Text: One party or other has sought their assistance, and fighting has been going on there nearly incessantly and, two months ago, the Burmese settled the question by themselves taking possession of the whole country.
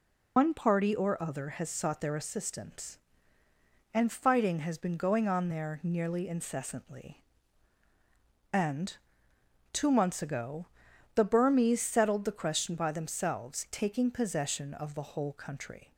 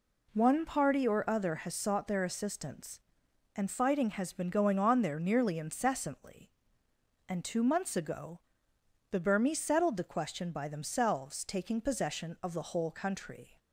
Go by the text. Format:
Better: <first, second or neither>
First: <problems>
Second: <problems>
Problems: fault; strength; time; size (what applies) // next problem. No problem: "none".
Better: second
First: loses the start of "One"; at 0.3 s; 155 ms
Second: none